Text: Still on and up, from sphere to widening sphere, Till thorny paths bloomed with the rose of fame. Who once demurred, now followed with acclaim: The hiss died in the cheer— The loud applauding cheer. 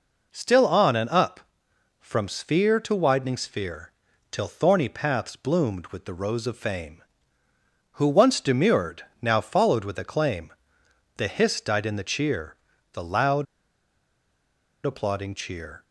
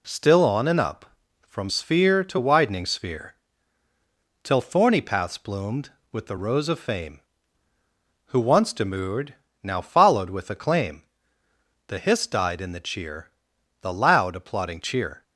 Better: second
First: pauses between "loud" and "applauding"; strong; at 13.4 s; 1.4 s long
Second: none

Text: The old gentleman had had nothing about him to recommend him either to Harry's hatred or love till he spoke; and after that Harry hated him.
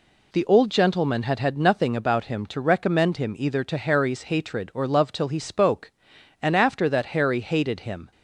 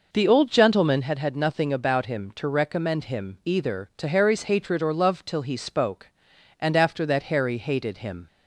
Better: first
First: none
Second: starts louder than the rest; noticeable; until 1.1 s; 5.5 dB

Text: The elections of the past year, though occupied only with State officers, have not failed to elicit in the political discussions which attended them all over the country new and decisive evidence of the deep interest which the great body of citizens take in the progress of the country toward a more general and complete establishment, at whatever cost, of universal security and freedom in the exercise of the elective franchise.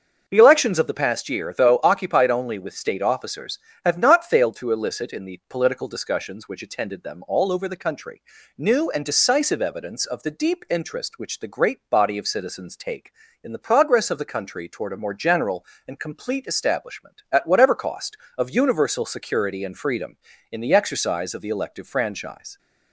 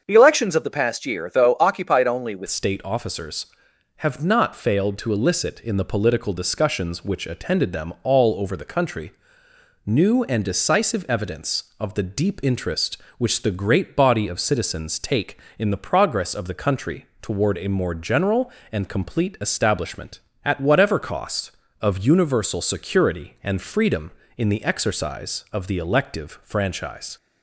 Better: first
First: starts louder than the rest; until 1.2 s; 6.5 dB // pauses between "country" and "new"; slight; at 8.2 s; 0.36 s long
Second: starts louder than the rest; until 1.0 s; 7 dB // changes voice at "State"; from 2.4 s on; 24.7 s long // pauses between "country" and "new"; noticeable; at 9.1 s; 0.74 s long // pauses between "country" and "toward"; slight; at 17.0 s; 0.16 s long

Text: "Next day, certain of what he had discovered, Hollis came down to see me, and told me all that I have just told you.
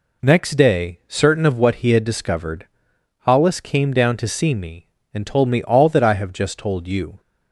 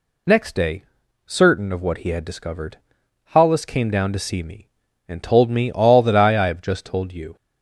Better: first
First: none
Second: says "I" twice; at 6.3 s

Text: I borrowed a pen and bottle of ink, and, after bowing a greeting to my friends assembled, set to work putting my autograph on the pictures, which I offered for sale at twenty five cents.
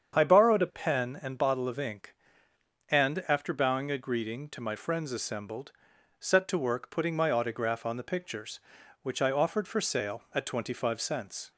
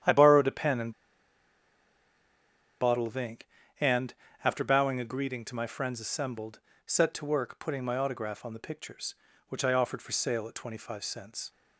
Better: first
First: starts louder than the rest; strong; until 1.2 s; 7.5 dB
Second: starts louder than the rest; strong; until 2.9 s; 10 dB // pauses between "and" and "bottle"; strong; at 0.9 s; 1.8 s long

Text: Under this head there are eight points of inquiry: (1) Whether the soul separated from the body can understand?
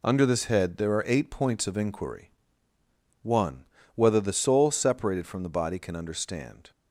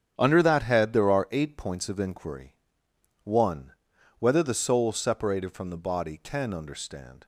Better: first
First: none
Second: starts louder than the rest; strong; until 1.1 s; 9 dB // says "that" for "this"; at 0.4 s

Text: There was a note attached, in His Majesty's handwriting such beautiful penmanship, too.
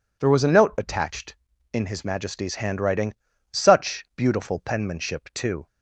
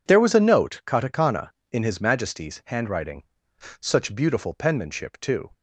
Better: first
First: pauses between "handwriting" and "such"; at 3.1 s; 0.40 s long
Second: says "katakana" for "attached"; at 0.8 s // pauses between "handwriting" and "such"; noticeable; at 3.2 s; 0.58 s long

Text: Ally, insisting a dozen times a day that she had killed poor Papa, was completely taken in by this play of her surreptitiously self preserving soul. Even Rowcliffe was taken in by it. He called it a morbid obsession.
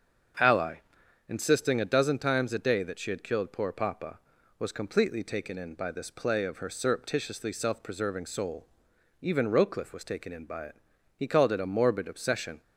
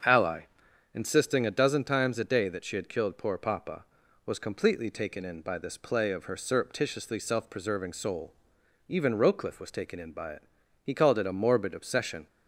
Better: neither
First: starts louder than the rest; until 1.9 s; 7 dB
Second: starts louder than the rest; until 1.5 s; 7 dB

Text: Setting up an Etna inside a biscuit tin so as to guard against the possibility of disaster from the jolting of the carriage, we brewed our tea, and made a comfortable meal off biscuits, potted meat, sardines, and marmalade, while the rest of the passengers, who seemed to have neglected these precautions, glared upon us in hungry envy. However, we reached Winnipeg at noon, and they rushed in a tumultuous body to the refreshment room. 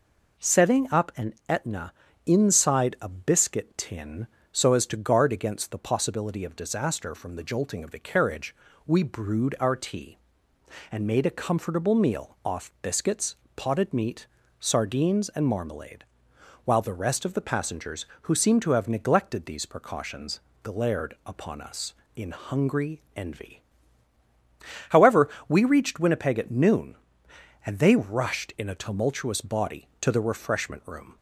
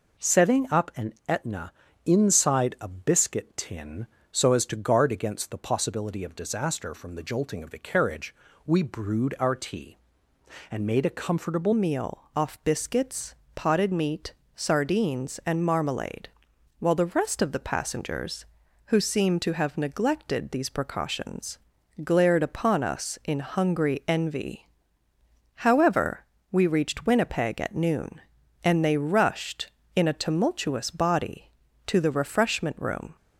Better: first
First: pauses between "an" and "Etna"; slight; at 1.3 s; 0.16 s long // pauses between "Etna" and "inside"; slight; at 1.9 s; 0.34 s long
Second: pauses between "an" and "Etna"; slight; at 1.1 s; 0.16 s long // pauses between "Etna" and "inside"; slight; at 1.7 s; 0.34 s long // changes voice at "meal"; from 11.7 s on; 21.4 s long

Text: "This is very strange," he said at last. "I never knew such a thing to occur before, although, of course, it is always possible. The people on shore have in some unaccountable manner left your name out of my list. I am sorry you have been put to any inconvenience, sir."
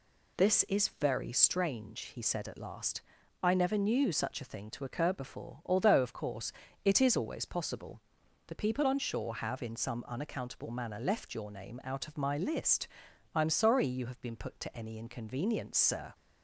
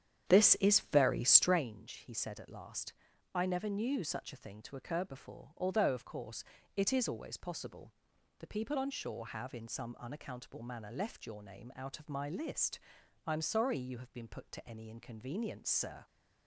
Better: first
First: none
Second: starts louder than the rest; strong; until 1.7 s; 9 dB

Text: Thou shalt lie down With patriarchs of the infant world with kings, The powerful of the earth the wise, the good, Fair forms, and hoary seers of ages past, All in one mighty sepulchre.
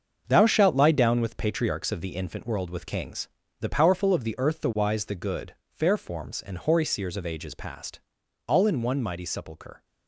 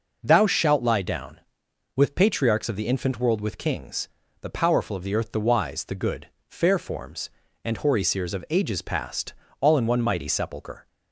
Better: second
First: gets quieter; strong; throughout; 9.5 dB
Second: none

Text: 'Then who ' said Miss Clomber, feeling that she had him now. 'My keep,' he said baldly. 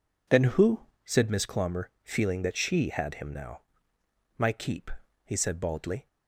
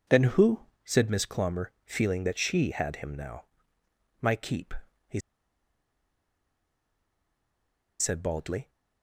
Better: first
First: none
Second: pauses between "he" and "said"; strong; at 5.2 s; 2.7 s long

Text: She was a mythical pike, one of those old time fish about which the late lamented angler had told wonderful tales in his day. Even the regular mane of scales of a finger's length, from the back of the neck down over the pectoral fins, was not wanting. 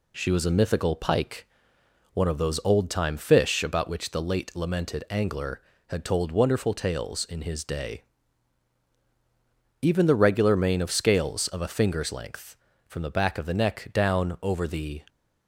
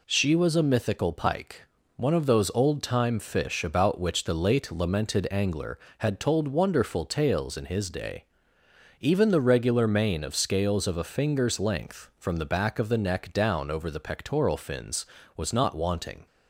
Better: second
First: stops before "pectoral fins was not wanting"; at 15.0 s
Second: none

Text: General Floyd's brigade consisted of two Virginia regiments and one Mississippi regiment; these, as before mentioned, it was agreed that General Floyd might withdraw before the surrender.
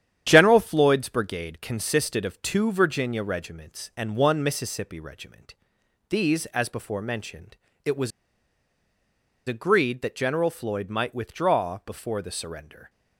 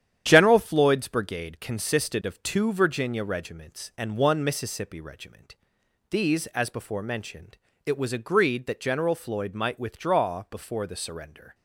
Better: second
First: starts louder than the rest; strong; until 1.2 s; 9.5 dB // pauses between "was" and "agreed"; strong; at 8.1 s; 1.3 s long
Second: starts louder than the rest; strong; until 1.2 s; 9.5 dB

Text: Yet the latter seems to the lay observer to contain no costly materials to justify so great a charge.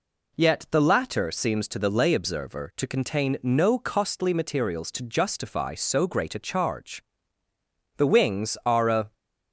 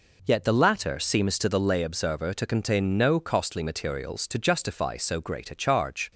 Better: second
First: goes on to say "The wings are a"; noticeable; from 7.9 s on; 1.1 s long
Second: none

